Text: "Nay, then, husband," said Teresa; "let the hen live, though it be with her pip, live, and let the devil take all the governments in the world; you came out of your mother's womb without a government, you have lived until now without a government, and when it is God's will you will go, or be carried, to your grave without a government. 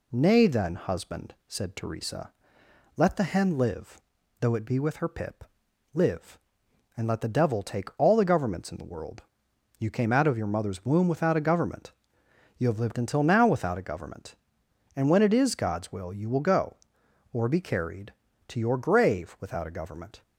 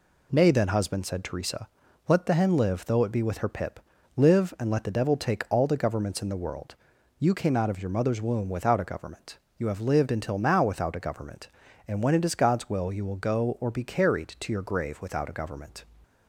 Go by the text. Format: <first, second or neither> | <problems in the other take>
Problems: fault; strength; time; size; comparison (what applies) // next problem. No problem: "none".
neither | none